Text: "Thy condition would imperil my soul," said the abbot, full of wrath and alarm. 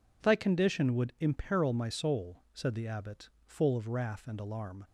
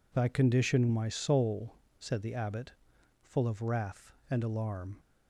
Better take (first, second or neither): first